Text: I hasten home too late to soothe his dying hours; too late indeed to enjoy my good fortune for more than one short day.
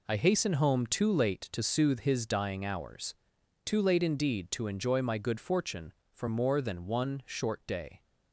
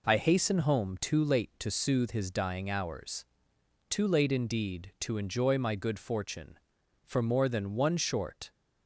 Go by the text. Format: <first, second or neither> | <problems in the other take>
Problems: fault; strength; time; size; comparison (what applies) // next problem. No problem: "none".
first | stops before "day"; at 8.5 s